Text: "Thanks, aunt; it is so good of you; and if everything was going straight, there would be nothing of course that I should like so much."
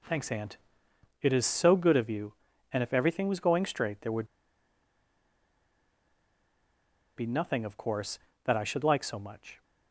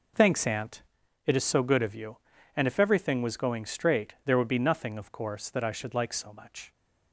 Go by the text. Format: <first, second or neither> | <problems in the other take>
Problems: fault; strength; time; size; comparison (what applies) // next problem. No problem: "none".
second | pauses between "would" and "be"; strong; at 4.2 s; 2.8 s long